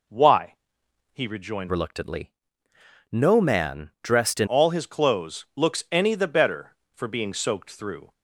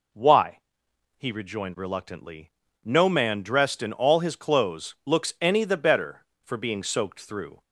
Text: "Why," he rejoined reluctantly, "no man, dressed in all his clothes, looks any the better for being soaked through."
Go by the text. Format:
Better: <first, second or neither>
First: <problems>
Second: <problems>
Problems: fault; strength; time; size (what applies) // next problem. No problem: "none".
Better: second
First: changes voice from "reluctantly" to "in"; from 1.6 to 4.4 s; 2.8 s long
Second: none